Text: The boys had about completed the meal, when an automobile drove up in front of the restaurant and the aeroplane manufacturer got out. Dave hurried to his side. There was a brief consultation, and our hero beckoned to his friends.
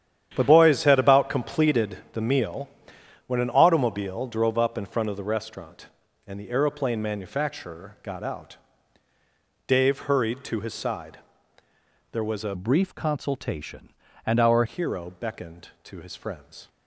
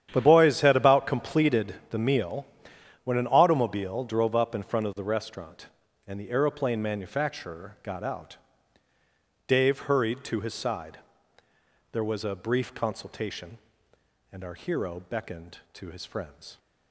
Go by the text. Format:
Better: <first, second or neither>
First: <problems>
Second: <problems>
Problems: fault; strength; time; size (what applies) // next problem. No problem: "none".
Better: second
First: starts louder than the rest; strong; until 1.3 s; 10 dB // pauses between "completed" and "the"; slight; at 1.9 s; 0.16 s long // changes voice from "brief" to "our"; from 12.5 to 14.6 s; 2.1 s long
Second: starts louder than the rest; strong; until 1.1 s; 10 dB // pauses between "completed" and "the"; slight; at 1.7 s; 0.16 s long